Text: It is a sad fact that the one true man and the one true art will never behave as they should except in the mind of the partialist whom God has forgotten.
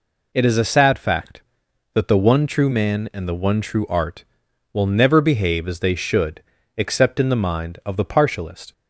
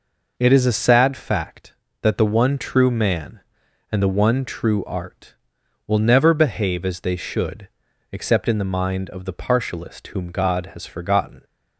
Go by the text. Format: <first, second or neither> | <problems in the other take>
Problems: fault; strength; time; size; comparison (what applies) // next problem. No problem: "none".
second | pauses between "should" and "except"; slight; at 6.4 s; 0.34 s long; also in the second // stops before "whom God has forgotten"; at 8.7 s